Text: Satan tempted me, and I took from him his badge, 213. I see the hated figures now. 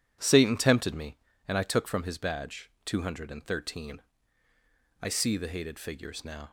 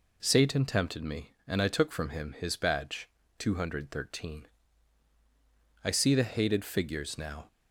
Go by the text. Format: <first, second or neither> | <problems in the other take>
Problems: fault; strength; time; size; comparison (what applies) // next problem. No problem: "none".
second | skips "him"; at 2.0 s